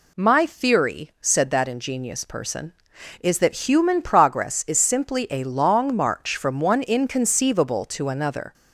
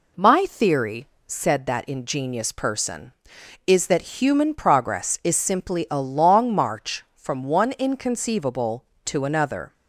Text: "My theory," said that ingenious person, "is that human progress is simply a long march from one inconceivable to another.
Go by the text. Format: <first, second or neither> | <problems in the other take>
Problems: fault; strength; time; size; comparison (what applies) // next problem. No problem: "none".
neither | none